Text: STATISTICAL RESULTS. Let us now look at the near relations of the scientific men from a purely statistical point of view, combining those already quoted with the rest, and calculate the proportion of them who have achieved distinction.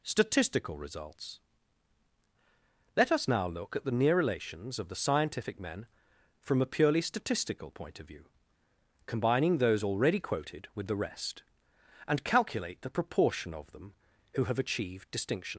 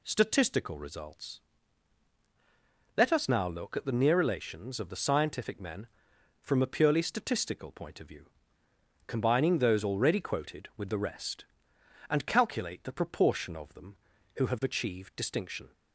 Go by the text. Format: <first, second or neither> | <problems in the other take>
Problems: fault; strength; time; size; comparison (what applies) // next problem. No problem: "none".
second | leaves "distinction" unfinished; at 15.5 s; 95 ms